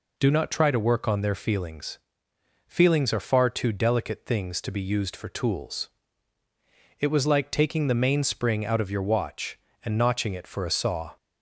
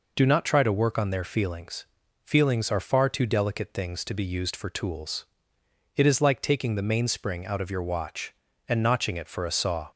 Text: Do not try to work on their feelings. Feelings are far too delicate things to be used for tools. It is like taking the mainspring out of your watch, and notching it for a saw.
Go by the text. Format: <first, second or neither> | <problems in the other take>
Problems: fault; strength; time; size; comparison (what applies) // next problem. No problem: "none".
second | says "was" for "is"; at 7.0 s